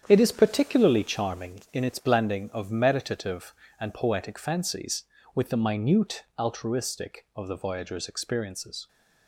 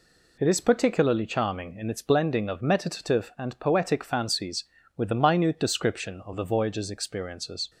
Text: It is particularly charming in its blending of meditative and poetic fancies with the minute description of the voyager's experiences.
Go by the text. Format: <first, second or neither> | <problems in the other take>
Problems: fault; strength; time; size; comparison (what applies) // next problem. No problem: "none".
second | starts louder than the rest; strong; until 1.0 s; 8.5 dB // says "altruistic" for "description"; at 6.3 s